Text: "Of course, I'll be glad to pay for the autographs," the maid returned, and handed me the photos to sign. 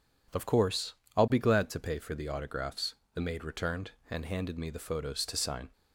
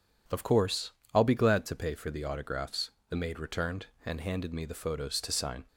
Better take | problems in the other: neither | none

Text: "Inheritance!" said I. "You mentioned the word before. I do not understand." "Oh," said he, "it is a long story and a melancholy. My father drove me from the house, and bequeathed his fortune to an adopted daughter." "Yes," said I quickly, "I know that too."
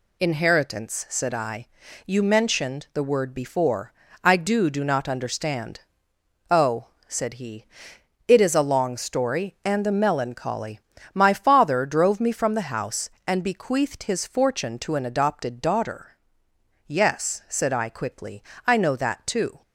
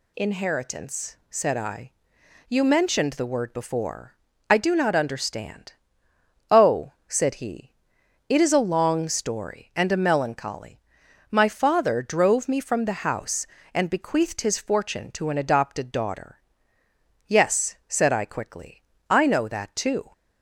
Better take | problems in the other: second | says "do" twice; at 4.6 s

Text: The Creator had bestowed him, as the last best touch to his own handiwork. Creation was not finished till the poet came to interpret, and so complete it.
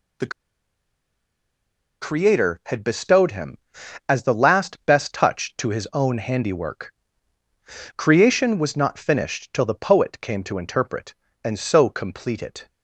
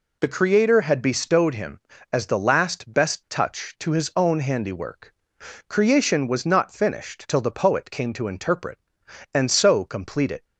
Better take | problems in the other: second | pauses between "The" and "Creator"; strong; at 0.3 s; 1.7 s long

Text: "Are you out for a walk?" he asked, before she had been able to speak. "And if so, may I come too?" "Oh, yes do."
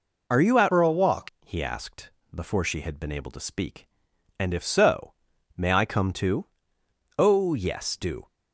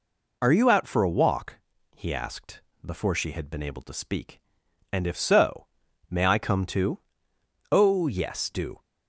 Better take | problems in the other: second | changes voice from "for" to "walk"; from 0.7 to 1.2 s; 0.5 s long

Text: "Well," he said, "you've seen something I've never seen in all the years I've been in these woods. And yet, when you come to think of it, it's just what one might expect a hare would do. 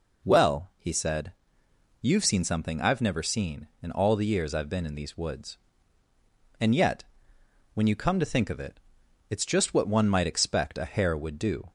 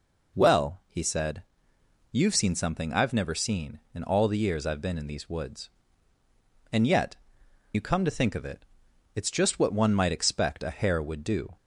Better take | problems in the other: first | skips "when"; at 7.4 s

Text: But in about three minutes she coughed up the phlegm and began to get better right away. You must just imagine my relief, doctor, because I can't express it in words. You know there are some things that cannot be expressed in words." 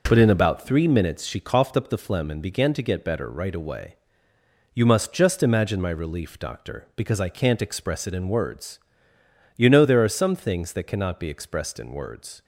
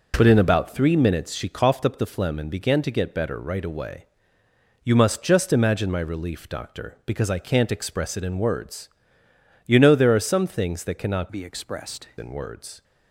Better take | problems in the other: first | changes voice from "be" to "expressed"; from 11.3 to 12.0 s; 0.7 s long

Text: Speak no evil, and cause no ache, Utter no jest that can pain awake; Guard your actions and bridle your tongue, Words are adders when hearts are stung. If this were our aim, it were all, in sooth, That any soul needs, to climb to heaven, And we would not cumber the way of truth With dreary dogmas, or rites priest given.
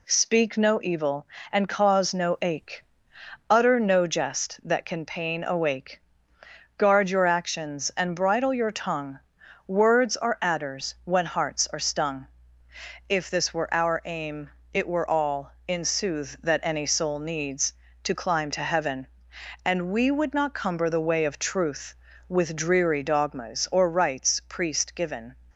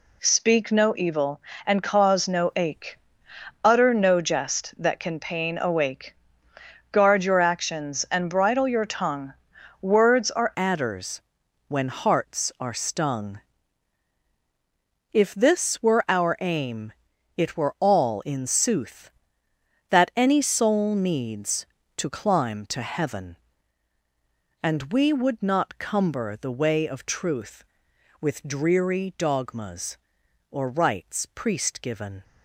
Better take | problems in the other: first | changes voice at "adders"; from 10.5 s on; 21.7 s long // pauses between "adders" and "when"; noticeable; at 11.2 s; 0.46 s long

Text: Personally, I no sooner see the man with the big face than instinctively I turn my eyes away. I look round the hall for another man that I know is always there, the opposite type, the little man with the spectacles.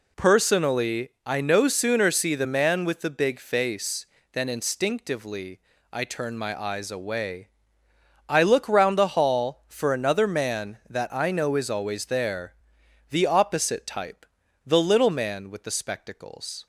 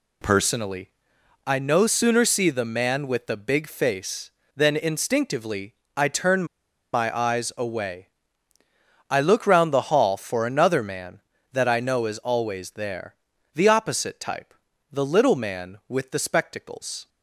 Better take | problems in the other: first | pauses between "instinctively" and "I"; slight; at 5.7 s; 0.22 s long; slight in the first // pauses between "turn" and "my"; noticeable; at 6.4 s; 0.48 s long

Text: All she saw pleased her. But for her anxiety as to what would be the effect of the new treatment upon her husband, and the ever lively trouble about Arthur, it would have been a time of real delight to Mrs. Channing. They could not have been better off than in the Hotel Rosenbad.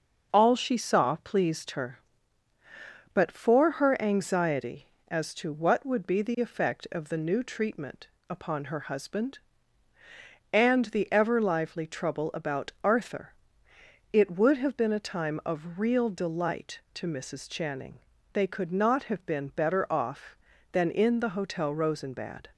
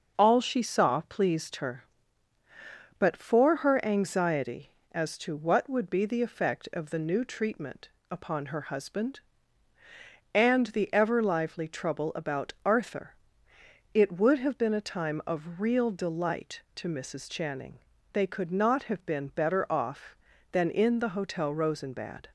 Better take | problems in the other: neither | starts louder than the rest; the same in both // pauses between "treatment" and "upon"; slight; the same in both

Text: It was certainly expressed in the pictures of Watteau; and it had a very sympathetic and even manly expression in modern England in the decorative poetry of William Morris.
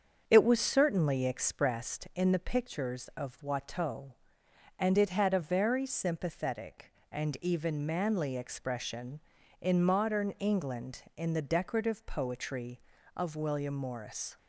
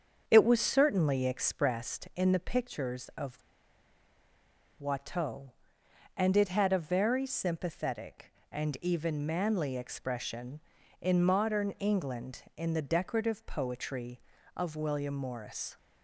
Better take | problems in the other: first | starts louder than the rest; until 1.2 s; 7 dB; also in the first // pauses between "of" and "Watteau"; strong; at 3.4 s; 1.3 s long

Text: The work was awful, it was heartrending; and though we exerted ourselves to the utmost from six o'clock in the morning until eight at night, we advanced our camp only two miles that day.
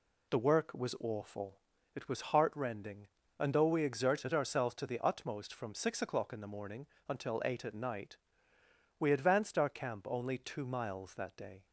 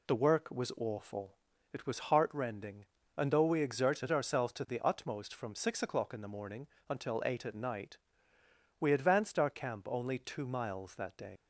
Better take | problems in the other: first | pauses between "morning" and "until"; slight; at 6.6 s; 0.20 s long; slight in the first // leaves "day" unfinished; at 11.3 s; 100 ms

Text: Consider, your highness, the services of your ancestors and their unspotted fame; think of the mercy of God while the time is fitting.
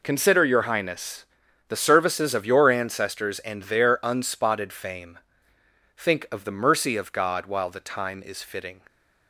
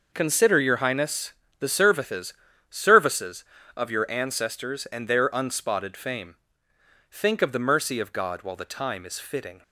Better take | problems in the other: first | says "services" twice; at 2.7 s

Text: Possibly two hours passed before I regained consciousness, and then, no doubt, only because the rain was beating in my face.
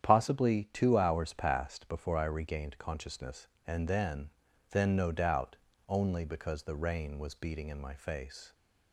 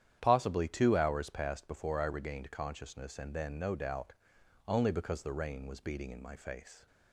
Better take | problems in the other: second | starts louder than the rest; strong; until 1.1 s; 9.5 dB; strong in the second // says "then" twice; at 4.7 s

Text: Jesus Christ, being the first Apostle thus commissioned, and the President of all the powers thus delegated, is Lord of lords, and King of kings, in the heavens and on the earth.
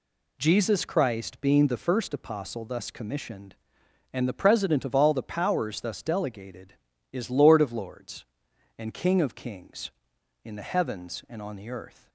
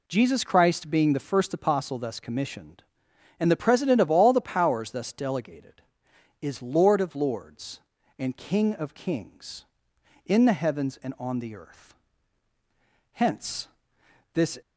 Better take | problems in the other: first | goes on to say "Hence this"; from 13.1 s on; 1.4 s long

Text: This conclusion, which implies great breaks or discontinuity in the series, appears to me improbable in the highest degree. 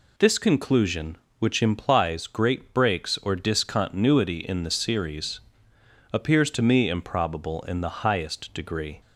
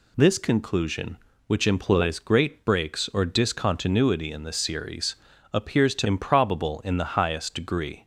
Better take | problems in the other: first | skips "me"; at 6.0 s

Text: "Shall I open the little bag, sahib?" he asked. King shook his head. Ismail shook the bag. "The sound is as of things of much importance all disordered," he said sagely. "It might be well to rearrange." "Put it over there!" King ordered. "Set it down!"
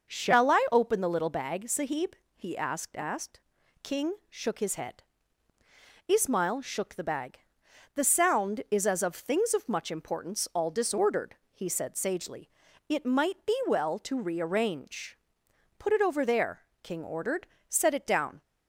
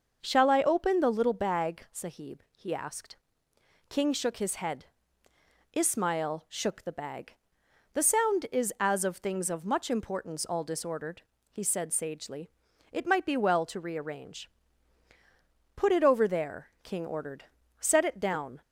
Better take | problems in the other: second | says "asked" twice; at 2.9 s // pauses between "King" and "shook"; slight; at 4.1 s; 0.16 s long

